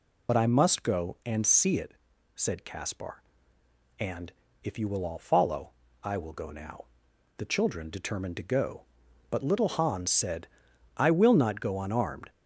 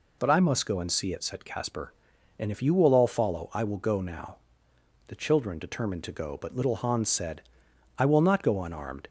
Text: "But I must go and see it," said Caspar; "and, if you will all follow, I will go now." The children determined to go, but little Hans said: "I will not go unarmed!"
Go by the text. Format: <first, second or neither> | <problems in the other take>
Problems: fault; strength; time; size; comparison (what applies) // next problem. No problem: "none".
second | loses the start of "But"; at 0.2 s; 60 ms